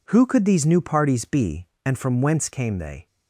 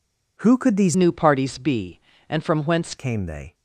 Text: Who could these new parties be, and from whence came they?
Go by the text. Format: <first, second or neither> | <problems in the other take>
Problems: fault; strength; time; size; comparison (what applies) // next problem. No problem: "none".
first | changes voice from "new" to "whence"; from 0.9 to 2.9 s; 2.0 s long